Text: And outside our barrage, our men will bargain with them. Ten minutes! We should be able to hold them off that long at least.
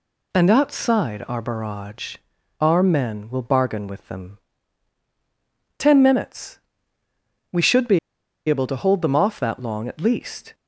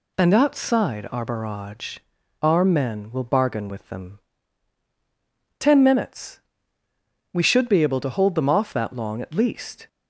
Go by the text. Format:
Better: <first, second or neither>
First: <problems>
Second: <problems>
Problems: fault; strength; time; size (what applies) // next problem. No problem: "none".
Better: second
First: pauses between "be" and "able"; noticeable; at 7.9 s; 0.49 s long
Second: none